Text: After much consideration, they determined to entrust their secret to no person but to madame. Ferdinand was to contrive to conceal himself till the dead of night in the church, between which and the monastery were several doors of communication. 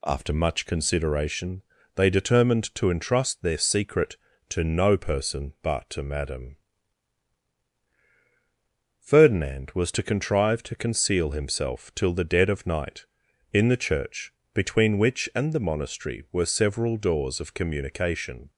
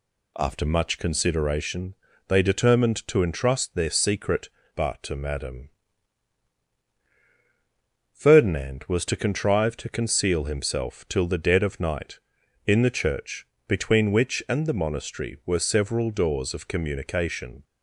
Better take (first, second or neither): first